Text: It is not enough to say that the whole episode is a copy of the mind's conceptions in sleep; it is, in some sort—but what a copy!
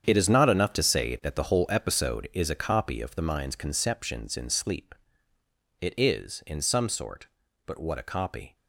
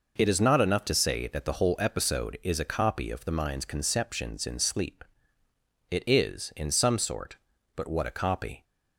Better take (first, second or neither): second